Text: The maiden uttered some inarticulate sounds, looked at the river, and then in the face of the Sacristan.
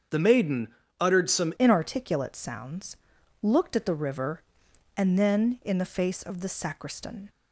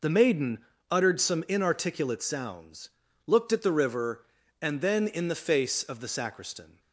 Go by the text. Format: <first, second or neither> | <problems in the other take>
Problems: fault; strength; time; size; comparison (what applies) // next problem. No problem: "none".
second | starts louder than the rest; strong; until 1.4 s; 7.5 dB // pauses between "maiden" and "uttered"; slight; at 0.6 s; 0.32 s long; slight in the second // changes voice at "inarticulate"; from 1.5 s on; 5.7 s long